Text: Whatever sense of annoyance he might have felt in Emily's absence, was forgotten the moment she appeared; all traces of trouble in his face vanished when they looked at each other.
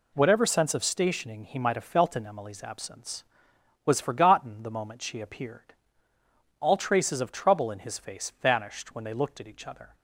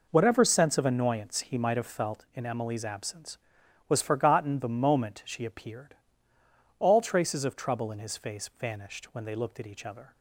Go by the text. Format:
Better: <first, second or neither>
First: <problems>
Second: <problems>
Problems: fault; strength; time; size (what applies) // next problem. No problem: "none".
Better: second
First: says "stationing" for "annoyance"; at 0.8 s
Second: none